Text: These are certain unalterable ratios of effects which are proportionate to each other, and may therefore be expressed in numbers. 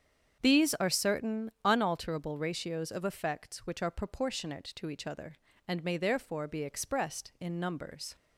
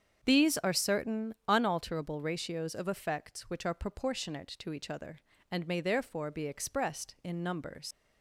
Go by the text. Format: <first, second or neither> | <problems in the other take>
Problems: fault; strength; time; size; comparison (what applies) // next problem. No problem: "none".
first | starts louder than the rest; strong; until 1.2 s; 7.5 dB; strong in the first // pauses between "certain" and "unalterable"; slight; at 1.3 s; 0.16 s long; slight in the first // leaves "numbers" unfinished; at 7.9 s; 75 ms